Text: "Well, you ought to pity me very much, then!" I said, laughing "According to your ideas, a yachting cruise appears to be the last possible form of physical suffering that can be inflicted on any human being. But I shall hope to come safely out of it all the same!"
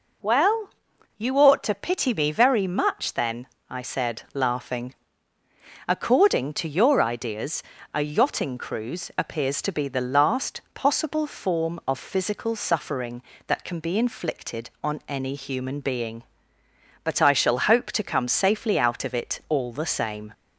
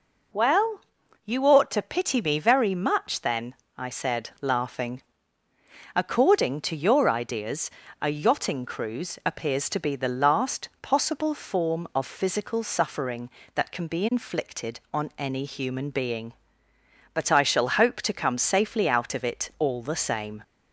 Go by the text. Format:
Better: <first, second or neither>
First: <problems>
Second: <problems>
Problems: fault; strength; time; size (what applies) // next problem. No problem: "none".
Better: neither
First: pauses between "laughing" and "According"; noticeable; at 4.9 s; 0.92 s long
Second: pauses between "laughing" and "According"; noticeable; at 5.0 s; 0.92 s long